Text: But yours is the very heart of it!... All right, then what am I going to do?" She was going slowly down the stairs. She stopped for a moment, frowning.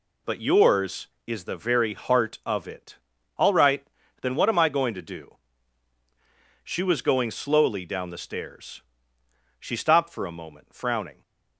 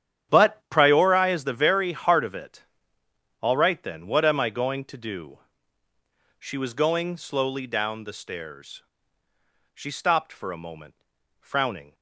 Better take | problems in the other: first | starts louder than the rest; strong; until 1.3 s; 10 dB // says "priori" for "yours"; at 0.6 s

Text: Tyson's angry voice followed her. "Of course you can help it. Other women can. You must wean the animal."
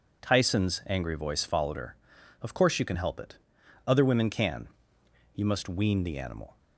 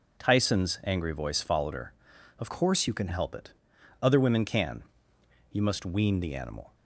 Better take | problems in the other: first | changes voice from "course" to "can"; from 2.4 to 3.0 s; 0.6 s long

